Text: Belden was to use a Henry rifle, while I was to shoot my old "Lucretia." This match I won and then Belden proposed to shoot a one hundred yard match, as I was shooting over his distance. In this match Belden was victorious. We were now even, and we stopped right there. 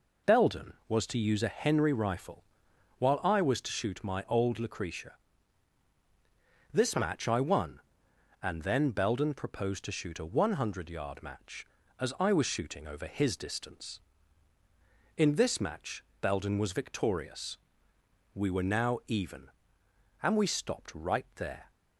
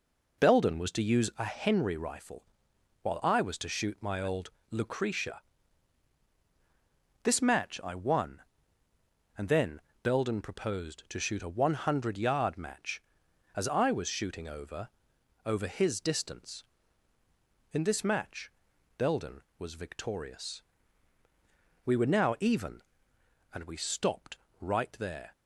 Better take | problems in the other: first | pauses between "old" and "Lucretia"; slight; at 4.5 s; 0.20 s long // pauses between "then" and "Belden"; slight; at 9.7 s; 0.24 s long // says "over" twice; at 15.4 s // pauses between "match" and "Belden"; noticeable; at 18.5 s; 0.46 s long; slight in the first // pauses between "stopped" and "right"; slight; at 24.3 s; 0.22 s long

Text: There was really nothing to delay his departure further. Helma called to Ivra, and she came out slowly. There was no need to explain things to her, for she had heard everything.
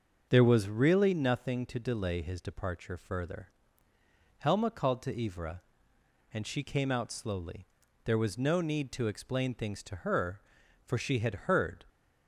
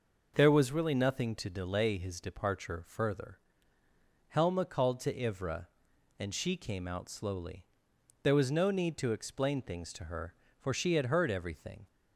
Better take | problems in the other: second | starts louder than the rest; until 1.3 s; 6.5 dB // stops before "everything"; at 11.8 s

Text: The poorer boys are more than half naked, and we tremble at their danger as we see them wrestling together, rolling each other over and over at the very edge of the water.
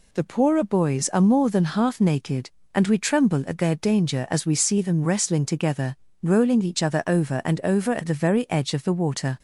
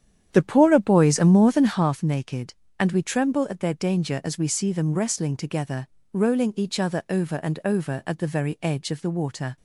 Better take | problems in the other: first | starts louder than the rest; strong; until 2.0 s; 9.5 dB

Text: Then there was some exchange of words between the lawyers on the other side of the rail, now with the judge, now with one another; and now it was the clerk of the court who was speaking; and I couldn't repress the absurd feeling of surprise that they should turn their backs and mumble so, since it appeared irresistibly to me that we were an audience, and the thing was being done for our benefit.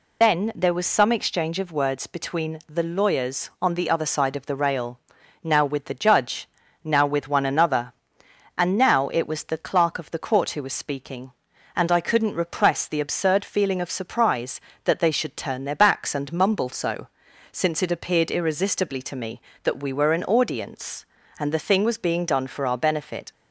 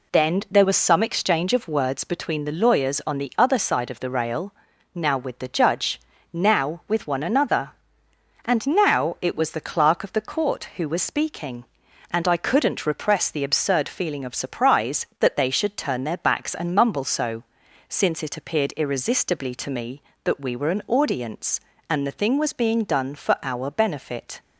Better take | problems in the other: second | loses the start of "Then"; at 0.2 s; 75 ms

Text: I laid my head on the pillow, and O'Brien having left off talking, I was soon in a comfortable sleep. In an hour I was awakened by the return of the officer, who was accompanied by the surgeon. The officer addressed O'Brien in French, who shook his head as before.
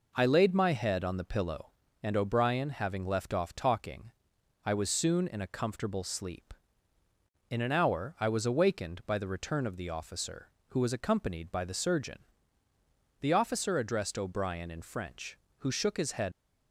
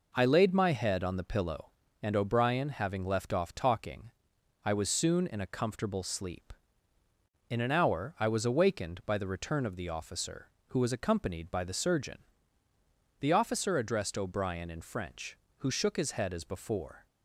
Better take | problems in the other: second | stops before "as before"; at 16.3 s

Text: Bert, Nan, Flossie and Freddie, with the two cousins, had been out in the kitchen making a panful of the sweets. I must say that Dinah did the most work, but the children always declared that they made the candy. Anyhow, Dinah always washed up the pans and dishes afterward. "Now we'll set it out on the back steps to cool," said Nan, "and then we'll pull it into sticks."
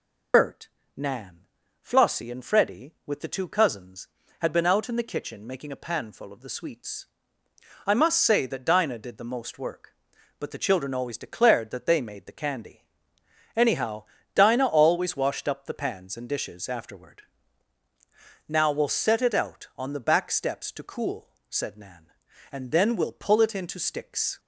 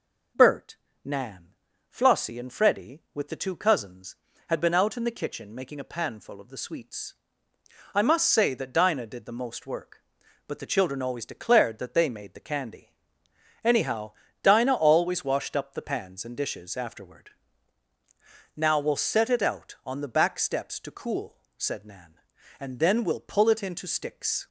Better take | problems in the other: second | loses the start of "Bert"; at 0.3 s; 70 ms

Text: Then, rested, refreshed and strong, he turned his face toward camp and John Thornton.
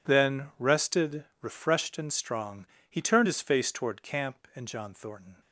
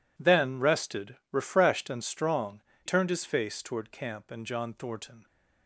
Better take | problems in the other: first | skips "he"; at 2.7 s

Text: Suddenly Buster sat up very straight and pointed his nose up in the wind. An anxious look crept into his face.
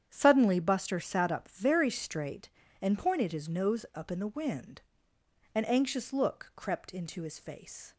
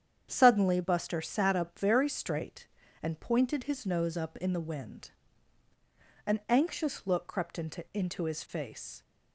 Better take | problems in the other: first | starts louder than the rest; strong; until 1.3 s; 8.5 dB; strong in the first // says "into" twice; at 7.9 s

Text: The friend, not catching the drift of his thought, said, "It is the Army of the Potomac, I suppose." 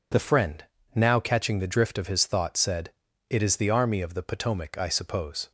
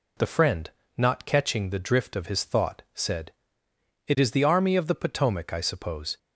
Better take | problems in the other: second | says "now" for "not"; at 0.9 s

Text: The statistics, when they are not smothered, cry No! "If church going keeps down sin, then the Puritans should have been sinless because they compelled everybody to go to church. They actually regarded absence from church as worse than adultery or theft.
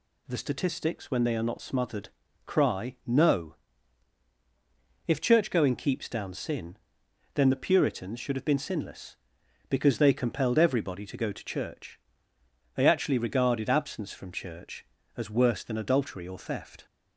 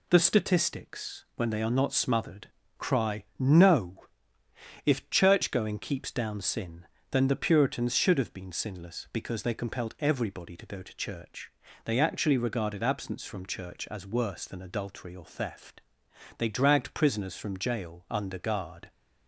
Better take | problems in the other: first | pauses between "cry" and "No"; slight; at 3.2 s; 0.16 s long // goes on to say "They dragged prisoners from jail under guard"; strong; from 16.3 s on; 2.5 s long

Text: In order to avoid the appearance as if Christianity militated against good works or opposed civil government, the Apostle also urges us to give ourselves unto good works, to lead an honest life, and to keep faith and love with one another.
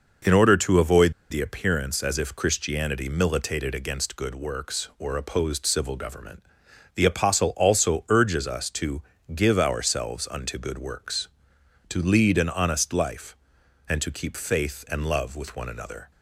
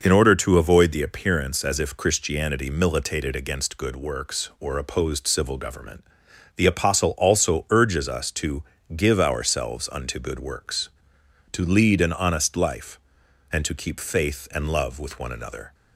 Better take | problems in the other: second | pauses between "avoid" and "the"; slight; at 1.1 s; 0.19 s long // pauses between "to" and "give"; slight; at 9.0 s; 0.32 s long; slight in the second

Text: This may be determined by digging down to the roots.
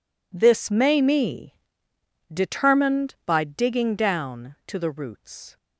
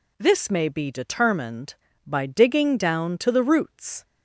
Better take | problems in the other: second | says "me" for "be"; at 1.0 s

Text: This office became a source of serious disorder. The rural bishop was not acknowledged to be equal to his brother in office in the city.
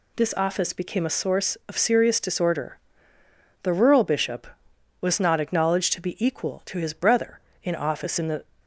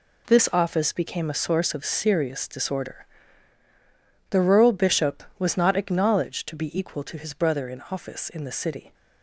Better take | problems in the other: second | stops before "city"; at 8.6 s

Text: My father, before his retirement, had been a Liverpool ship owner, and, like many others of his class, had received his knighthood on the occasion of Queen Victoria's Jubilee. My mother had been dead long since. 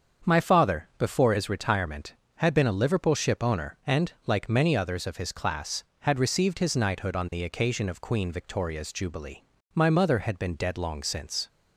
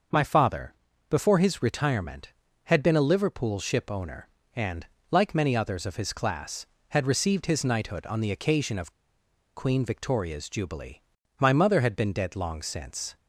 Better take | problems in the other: first | starts louder than the rest; until 1.4 s; 6 dB; strong in the first // pauses between "of" and "Queen"; noticeable; at 8.9 s; 0.64 s long

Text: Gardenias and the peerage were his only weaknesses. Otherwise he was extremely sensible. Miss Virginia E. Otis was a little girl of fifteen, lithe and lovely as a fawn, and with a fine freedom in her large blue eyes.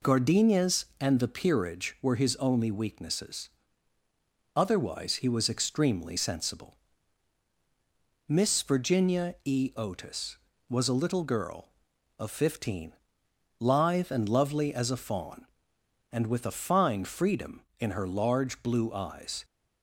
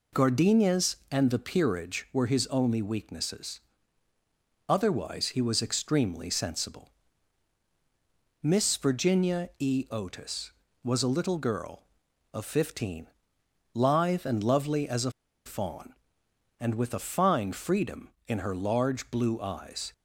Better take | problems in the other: first | pauses between "a" and "fawn"; slight; at 15.0 s; 0.35 s long

